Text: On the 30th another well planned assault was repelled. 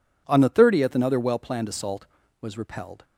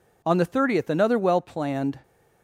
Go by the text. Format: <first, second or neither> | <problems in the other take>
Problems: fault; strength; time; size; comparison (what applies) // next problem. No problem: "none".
first | stops before "assault was repelled"; at 2.0 s